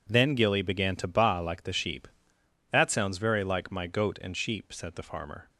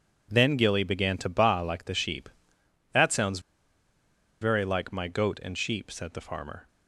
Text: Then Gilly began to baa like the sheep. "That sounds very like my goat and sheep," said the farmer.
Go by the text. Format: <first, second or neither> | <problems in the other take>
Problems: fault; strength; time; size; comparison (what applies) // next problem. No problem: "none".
first | pauses between "sounds" and "very"; at 3.3 s; 1.0 s long